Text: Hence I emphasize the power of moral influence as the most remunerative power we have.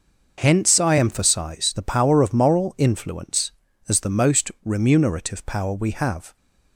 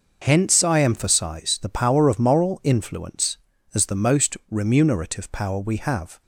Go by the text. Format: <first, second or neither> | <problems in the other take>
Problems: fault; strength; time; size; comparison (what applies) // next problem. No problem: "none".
neither | none